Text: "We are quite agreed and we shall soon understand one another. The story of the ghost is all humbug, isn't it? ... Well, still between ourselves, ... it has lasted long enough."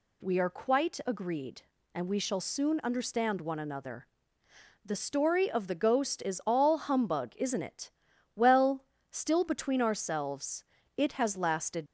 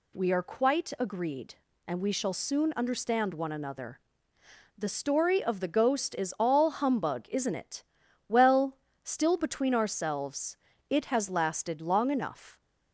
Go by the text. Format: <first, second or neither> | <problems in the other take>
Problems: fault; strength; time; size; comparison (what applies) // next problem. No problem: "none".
second | stops before "long enough"; at 11.8 s